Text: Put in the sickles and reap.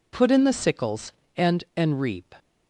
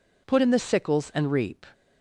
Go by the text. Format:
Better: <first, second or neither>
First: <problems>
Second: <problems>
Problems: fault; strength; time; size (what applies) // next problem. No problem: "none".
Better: second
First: says "and" twice; at 1.7 s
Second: none